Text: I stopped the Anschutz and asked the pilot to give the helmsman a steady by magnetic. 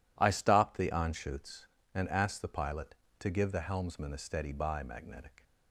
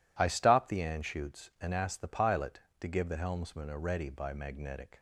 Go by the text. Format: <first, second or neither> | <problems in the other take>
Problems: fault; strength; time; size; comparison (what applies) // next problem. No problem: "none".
first | says "ready" for "steady"; at 3.7 s